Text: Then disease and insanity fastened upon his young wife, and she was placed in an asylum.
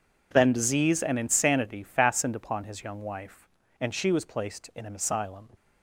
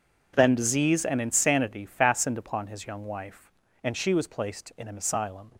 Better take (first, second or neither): neither